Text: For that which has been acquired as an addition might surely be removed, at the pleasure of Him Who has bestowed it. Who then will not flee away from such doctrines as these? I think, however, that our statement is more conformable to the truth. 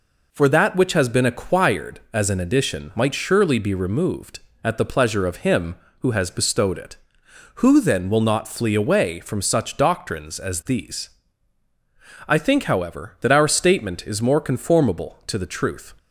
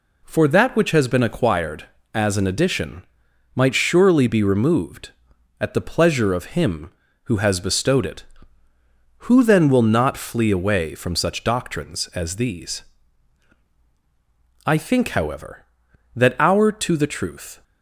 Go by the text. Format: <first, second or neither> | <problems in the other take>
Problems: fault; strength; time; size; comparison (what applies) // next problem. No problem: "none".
first | pauses between "addition" and "might"; noticeable; at 3.0 s; 0.50 s long // skips "statement is more conformable"; at 16.7 s